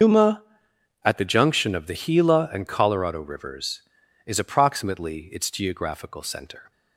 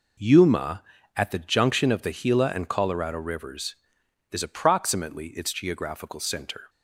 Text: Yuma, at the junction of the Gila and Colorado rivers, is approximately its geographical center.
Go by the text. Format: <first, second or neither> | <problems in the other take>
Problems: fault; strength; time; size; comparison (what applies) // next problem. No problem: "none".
second | loses the start of "Yuma"; at 0.0 s; 125 ms // starts louder than the rest; until 1.6 s; 6.5 dB